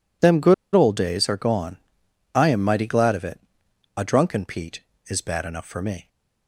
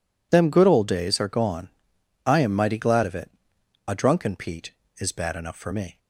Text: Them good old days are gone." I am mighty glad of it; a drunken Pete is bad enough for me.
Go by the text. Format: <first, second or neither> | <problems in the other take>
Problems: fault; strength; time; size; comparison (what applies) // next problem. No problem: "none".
second | pauses between "good" and "old"; slight; at 0.5 s; 0.21 s long